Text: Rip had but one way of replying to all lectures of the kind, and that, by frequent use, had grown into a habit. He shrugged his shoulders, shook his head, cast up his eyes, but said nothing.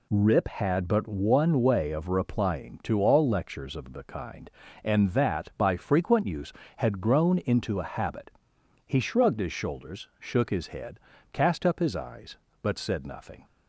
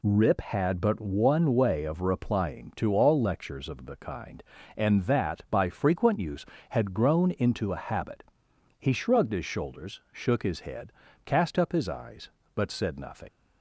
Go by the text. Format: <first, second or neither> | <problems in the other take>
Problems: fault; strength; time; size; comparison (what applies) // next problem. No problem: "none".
first | leaves "nothing" unfinished; at 13.2 s; 95 ms